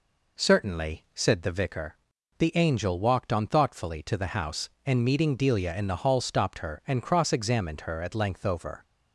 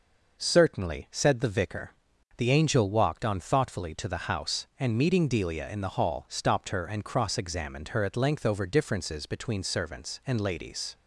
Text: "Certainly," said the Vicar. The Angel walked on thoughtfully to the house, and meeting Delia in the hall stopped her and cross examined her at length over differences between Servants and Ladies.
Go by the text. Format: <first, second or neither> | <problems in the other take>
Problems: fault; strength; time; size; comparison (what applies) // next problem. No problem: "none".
second | stops before "differences between Servants and Ladies"; at 8.8 s